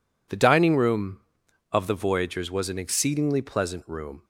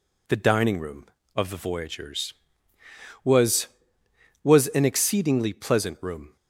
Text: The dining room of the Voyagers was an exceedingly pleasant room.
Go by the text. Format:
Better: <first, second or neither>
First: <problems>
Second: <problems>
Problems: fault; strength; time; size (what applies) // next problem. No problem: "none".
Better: first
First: none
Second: says "was" twice; at 4.4 s